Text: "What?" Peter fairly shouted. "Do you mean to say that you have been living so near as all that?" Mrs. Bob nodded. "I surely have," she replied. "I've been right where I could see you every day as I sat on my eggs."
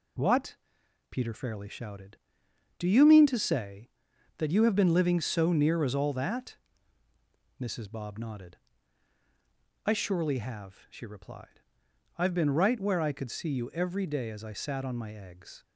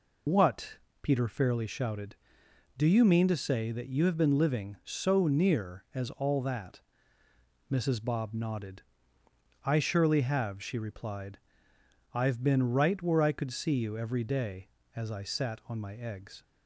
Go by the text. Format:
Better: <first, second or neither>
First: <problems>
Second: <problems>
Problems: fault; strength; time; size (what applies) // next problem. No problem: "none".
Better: first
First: none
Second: loses the start of "What"; at 0.2 s; 60 ms